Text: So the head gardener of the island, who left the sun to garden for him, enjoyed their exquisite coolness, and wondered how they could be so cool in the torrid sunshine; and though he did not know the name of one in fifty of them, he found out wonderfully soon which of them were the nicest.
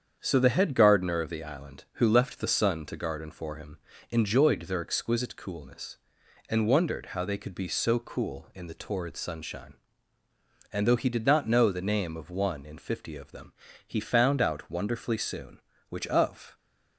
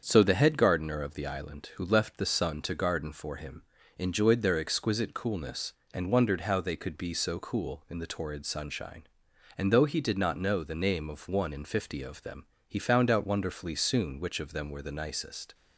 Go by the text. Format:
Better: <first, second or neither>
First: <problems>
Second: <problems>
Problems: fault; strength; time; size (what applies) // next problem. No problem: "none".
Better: second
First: starts louder than the rest; strong; until 1.2 s; 8 dB // stops before "them were the nicest"; at 16.5 s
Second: starts louder than the rest; strong; until 1.0 s; 7 dB